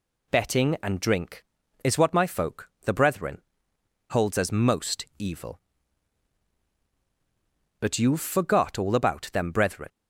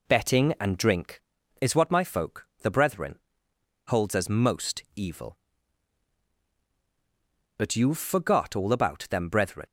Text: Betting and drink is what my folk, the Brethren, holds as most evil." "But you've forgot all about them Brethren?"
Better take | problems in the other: first | starts louder than the rest; slight; until 1.3 s; 2.5 dB

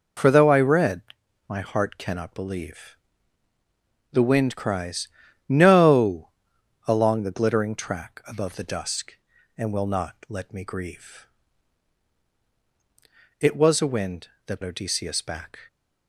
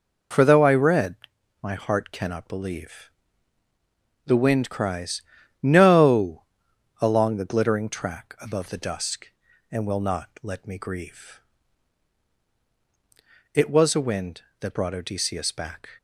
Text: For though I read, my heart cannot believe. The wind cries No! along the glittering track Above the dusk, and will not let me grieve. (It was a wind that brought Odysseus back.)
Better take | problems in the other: second | pauses between "cries" and "No"; at 5.0 s; 0.42 s long; also in the second // skips "brought"; at 14.6 s

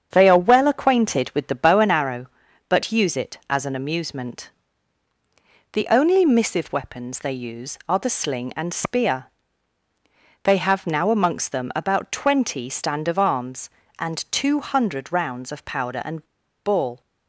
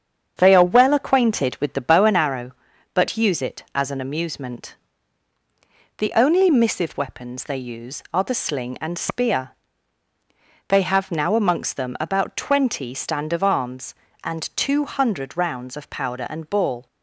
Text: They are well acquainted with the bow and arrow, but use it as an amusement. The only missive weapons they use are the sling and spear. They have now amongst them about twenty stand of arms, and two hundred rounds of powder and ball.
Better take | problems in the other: second | starts louder than the rest; strong; until 1.1 s; 7.5 dB; strong in the second // pauses between "and" and "ball"; at 16.2 s; 0.39 s long

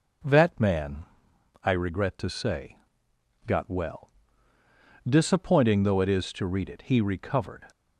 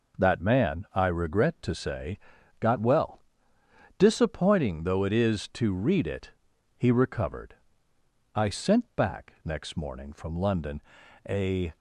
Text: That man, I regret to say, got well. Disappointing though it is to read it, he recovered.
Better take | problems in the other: first | goes on to say "I sent back next morning from London a"; strong; from 8.3 s on; 3.4 s long

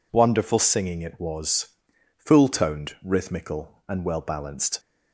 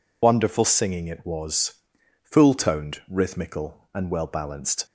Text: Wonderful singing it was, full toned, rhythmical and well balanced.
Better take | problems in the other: first | loses the start of "Wonderful"; at 0.2 s; 55 ms

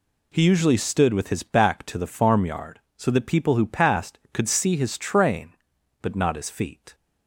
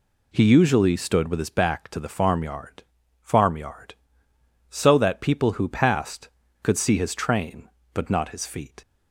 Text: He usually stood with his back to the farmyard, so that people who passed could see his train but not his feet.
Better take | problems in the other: first | says "farmyard" twice; at 3.2 s

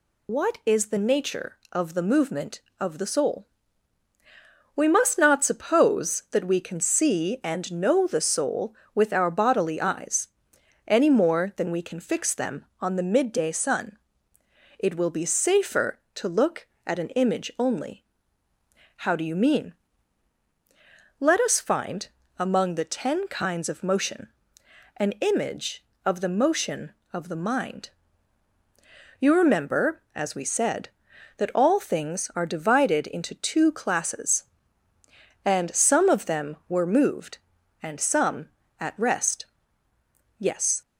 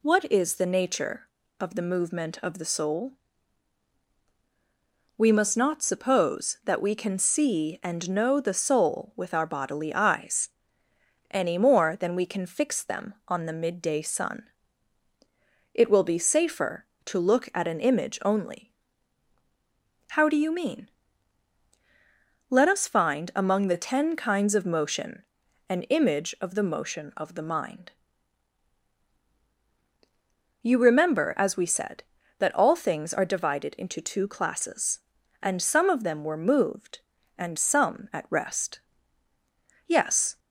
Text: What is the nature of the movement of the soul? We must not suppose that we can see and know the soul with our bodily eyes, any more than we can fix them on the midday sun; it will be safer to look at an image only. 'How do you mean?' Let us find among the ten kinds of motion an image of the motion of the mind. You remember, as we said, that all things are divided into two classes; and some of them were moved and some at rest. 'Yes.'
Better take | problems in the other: second | loses the start of "What"; at 0.2 s; 50 ms // pauses between "find" and "among"; slight; at 22.0 s; 0.28 s long // pauses between "motion" and "an"; noticeable; at 24.2 s; 0.68 s long; also in the second

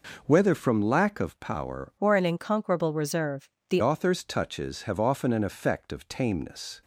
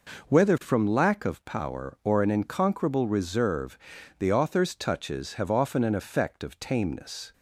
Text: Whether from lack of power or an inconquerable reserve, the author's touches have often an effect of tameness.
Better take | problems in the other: second | changes voice from "or" to "the"; from 1.9 to 3.8 s; 1.9 s long

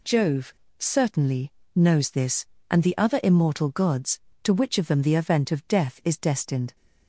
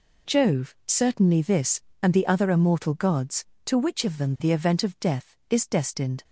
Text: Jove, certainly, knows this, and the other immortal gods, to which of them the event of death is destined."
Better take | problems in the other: first | skips "knows"; at 1.4 s

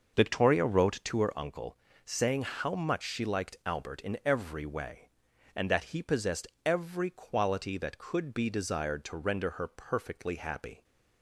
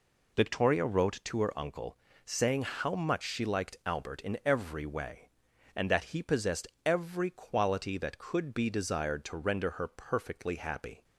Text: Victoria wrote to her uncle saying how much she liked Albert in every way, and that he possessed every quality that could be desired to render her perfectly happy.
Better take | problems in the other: second | starts louder than the rest; noticeable; until 1.4 s; 6 dB // pauses between "uncle" and "saying"; slight; at 1.7 s; 0.30 s long; slight in the second // pauses between "possessed" and "every"; slight; at 6.4 s; 0.18 s long; slight in the second

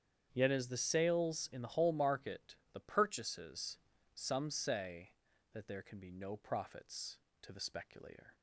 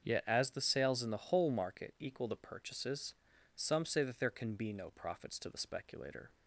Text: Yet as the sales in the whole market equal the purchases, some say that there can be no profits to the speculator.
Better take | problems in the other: second | starts louder than the rest; strong; until 1.3 s; 8.5 dB; also in the second // skips "equal"; at 2.6 s

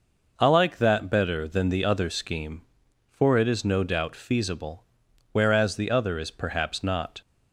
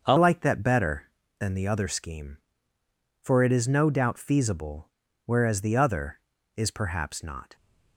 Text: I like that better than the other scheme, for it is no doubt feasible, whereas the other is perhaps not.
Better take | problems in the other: first | starts louder than the rest; until 1.0 s; 6.5 dB // changes voice at "like"; from 0.1 s on; 7.4 s long

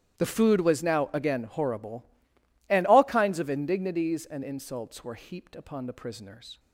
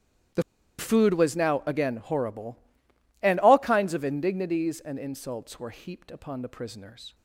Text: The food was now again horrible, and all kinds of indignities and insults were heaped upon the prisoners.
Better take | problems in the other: first | starts louder than the rest; strong; until 1.7 s; 12 dB; strong in the first // pauses between "The" and "food"; at 0.4 s; 0.36 s long

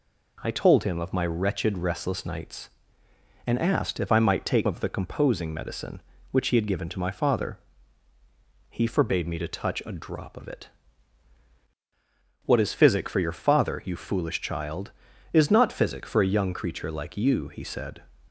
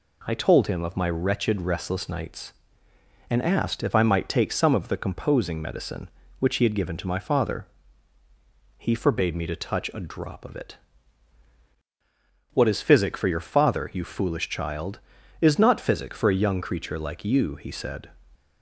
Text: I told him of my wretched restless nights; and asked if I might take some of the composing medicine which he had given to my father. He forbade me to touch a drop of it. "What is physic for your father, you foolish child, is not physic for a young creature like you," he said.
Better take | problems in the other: second | skips "some"; at 4.6 s

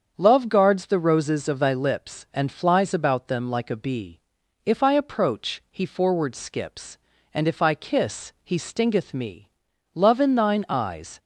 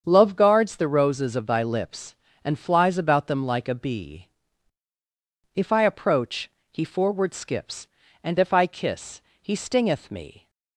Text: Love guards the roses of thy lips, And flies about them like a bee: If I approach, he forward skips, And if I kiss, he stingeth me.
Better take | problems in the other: second | starts louder than the rest; strong; until 1.1 s; 7 dB; strong in the second // goes on to say "Love in thine eyes"; noticeable; from 9.9 s on; 1.2 s long

